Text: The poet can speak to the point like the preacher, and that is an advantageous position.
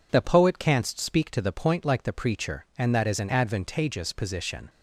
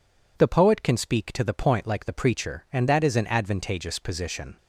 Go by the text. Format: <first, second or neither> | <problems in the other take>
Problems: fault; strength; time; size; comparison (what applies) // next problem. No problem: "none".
second | says "canst" for "can"; at 0.5 s